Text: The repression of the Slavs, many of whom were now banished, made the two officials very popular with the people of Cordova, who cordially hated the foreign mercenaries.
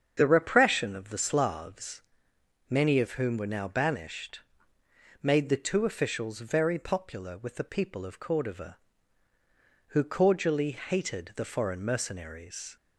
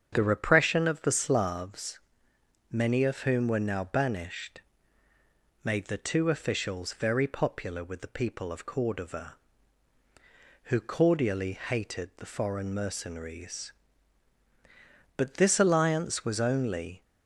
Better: first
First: starts louder than the rest; strong; until 1.1 s; 7.5 dB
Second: starts louder than the rest; strong; until 1.1 s; 7.5 dB // goes on to say "But this alliance was only"; strong; from 15.1 s on; 1.8 s long

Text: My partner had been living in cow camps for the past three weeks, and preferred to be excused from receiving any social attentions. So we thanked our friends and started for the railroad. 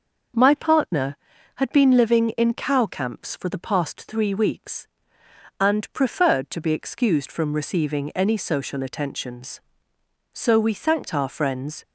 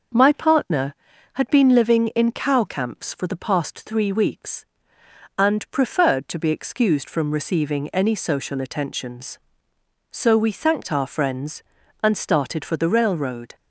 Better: second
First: stops before "and started for the railroad"; at 11.8 s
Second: none

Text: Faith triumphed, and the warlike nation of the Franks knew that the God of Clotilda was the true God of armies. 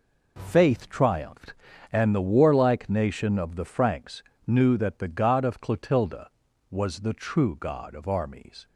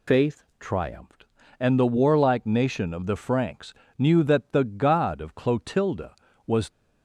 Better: first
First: pauses between "Franks" and "knew"; slight; at 4.2 s; 0.22 s long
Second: pauses between "Faith" and "triumphed"; slight; at 0.4 s; 0.16 s long // pauses between "Franks" and "knew"; slight; at 3.7 s; 0.24 s long // stops before "the true God of armies"; at 6.7 s

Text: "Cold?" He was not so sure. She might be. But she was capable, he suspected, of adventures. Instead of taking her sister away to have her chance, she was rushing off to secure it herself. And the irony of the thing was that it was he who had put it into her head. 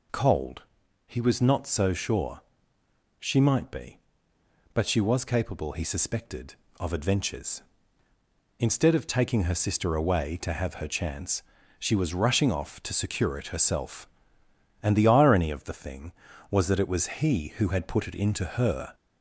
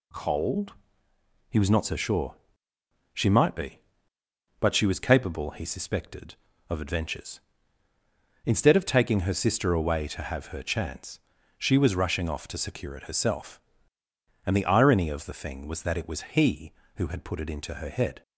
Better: second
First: stops before "head"; at 18.9 s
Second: none

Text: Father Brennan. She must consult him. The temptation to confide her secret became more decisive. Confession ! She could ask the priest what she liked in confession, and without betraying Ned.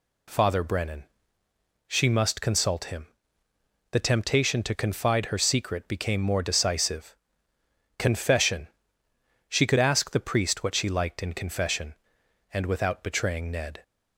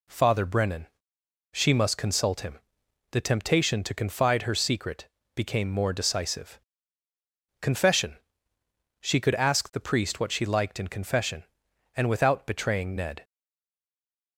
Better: first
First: none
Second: pauses between "secret" and "became"; slight; at 5.0 s; 0.28 s long // stays silent after the last word; from 13.2 s on; 1.1 s long

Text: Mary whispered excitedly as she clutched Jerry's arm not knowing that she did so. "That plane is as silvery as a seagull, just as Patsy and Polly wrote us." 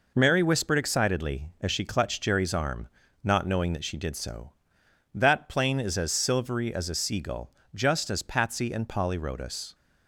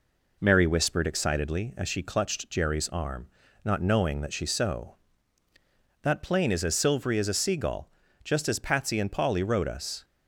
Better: first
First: pauses between "arm" and "not"; at 2.8 s; 0.38 s long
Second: pauses between "arm" and "not"; slight; at 3.2 s; 0.36 s long // skips "did"; at 4.4 s

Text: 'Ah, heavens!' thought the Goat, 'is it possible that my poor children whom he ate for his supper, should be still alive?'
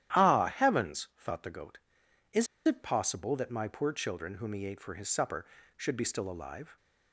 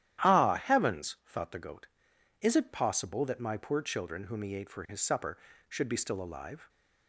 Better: second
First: starts louder than the rest; strong; until 1.2 s; 12 dB // pauses between "is" and "it"; slight; at 2.4 s; 0.20 s long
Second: starts louder than the rest; strong; until 1.3 s; 12 dB

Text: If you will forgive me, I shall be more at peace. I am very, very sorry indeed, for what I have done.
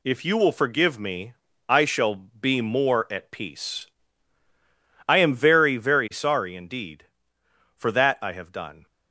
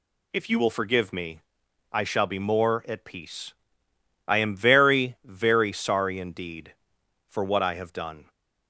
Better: second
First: says "that" for "what"; at 7.9 s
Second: none

